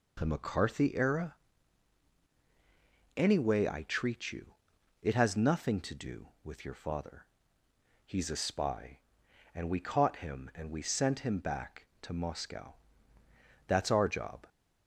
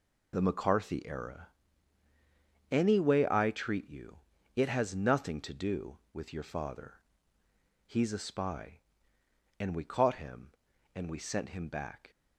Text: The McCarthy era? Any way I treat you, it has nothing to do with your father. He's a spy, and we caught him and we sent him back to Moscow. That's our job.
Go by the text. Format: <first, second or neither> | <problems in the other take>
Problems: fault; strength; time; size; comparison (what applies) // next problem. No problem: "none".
first | stops before "to Moscow That's our job"; at 12.1 s